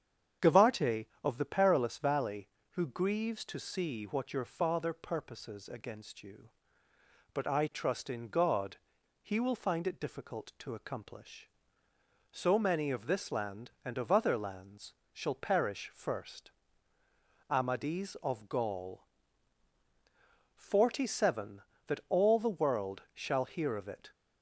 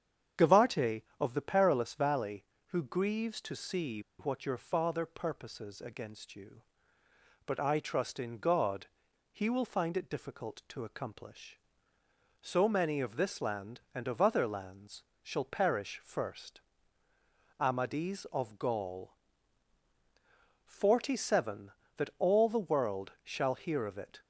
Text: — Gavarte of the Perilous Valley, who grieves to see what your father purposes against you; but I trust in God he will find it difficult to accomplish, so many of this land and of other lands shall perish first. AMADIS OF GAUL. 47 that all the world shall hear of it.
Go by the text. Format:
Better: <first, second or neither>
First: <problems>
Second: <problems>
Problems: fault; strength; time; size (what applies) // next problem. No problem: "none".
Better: first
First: starts louder than the rest; strong; until 1.6 s; 8 dB // pauses between "God" and "he"; at 8.7 s; 0.44 s long // pauses between "lands" and "shall"; slight; at 14.9 s; 0.20 s long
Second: starts louder than the rest; strong; until 1.5 s; 8.5 dB // pauses between "see" and "what"; slight; at 4.0 s; 0.18 s long // pauses between "God" and "he"; at 8.8 s; 0.44 s long // pauses between "lands" and "shall"; slight; at 15.0 s; 0.20 s long